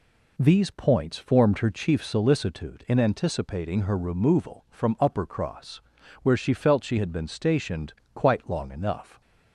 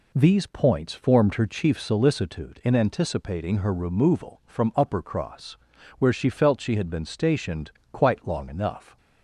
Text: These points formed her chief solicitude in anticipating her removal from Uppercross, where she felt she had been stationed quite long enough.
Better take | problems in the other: neither | pauses between "stationed" and "quite"; slight; the same in both

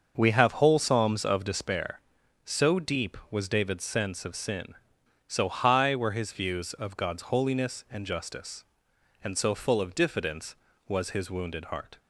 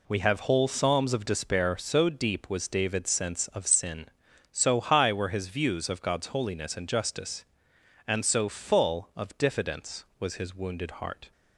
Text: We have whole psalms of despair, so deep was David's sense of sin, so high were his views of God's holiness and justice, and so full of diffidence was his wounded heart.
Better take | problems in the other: second | starts louder than the rest; until 1.7 s; 6.5 dB

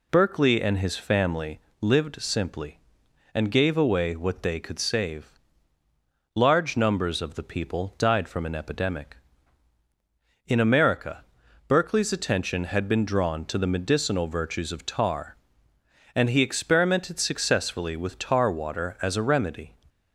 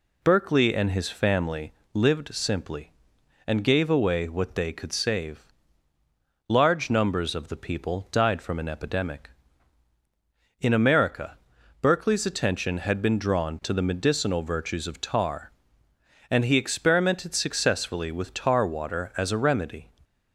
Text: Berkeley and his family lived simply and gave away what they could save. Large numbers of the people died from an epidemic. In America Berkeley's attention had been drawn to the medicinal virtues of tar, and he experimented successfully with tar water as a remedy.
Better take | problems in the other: neither | pauses between "family" and "lived"; slight; the same in both // pauses between "America" and "Berkeley's"; the same in both

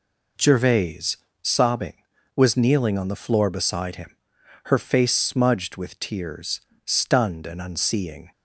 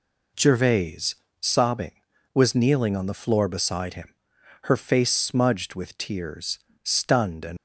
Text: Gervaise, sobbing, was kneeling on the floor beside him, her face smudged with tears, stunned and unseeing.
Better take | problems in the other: first | stops before "unseeing"; at 7.5 s

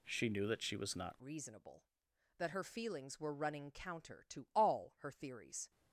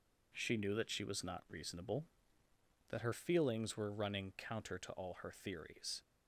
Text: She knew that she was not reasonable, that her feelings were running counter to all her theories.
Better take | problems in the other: second | changes voice at "reasonable"; from 1.2 s on; 4.5 s long

